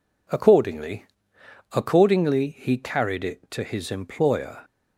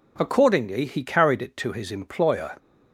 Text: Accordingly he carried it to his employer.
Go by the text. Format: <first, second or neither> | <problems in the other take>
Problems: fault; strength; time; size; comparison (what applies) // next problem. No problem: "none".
second | says "Accordingly" twice; at 1.7 s